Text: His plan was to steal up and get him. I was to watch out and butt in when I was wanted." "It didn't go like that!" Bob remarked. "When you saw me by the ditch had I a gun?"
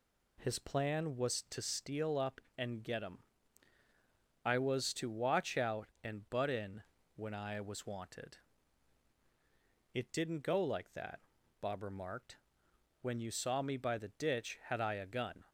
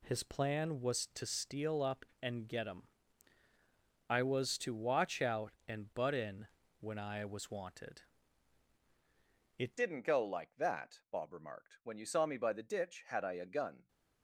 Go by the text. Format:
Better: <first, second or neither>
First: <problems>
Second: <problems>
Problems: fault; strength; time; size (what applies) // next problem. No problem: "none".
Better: first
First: pauses between "in" and "when"; slight; at 6.8 s; 0.34 s long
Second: pauses between "in" and "when"; slight; at 6.4 s; 0.34 s long // changes voice at "didn't"; from 9.7 s on; 4.1 s long